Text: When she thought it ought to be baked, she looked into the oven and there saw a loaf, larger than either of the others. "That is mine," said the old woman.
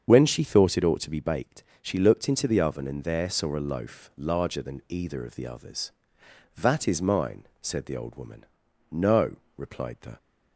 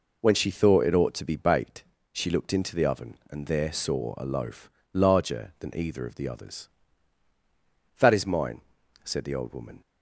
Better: second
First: starts louder than the rest; strong; until 1.1 s; 7 dB // goes on to say "No replied the"; noticeable; from 8.9 s on; 1.2 s long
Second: none

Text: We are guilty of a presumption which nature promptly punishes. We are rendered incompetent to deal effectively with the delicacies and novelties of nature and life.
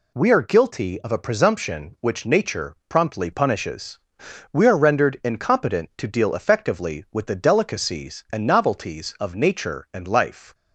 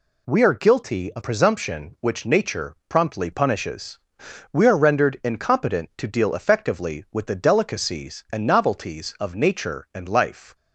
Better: first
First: none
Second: skips "a"; at 1.2 s

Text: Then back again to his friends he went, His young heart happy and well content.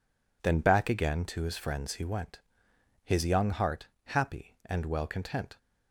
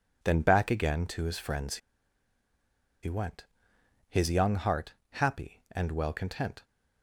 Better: first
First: pauses between "heart" and "happy"; slight; at 3.8 s; 0.16 s long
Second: pauses between "friends" and "he"; strong; at 1.7 s; 1.2 s long // pauses between "heart" and "happy"; slight; at 4.9 s; 0.16 s long

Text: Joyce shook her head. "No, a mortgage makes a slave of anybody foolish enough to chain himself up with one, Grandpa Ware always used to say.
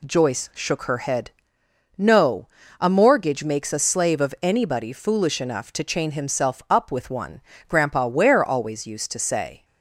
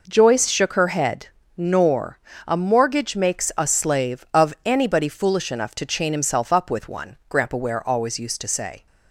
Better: first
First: none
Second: says "Nor" for "No"; at 1.5 s

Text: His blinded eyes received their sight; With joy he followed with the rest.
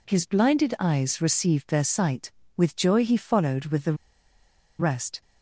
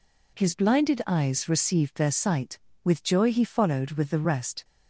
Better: second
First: pauses between "the" and "rest"; noticeable; at 3.9 s; 0.84 s long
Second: none

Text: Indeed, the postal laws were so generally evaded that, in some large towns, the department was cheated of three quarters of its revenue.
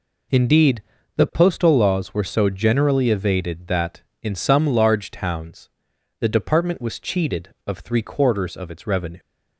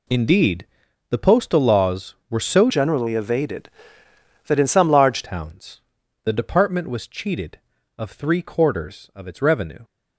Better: first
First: none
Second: changes voice from "generally" to "large"; from 2.6 to 5.2 s; 2.6 s long

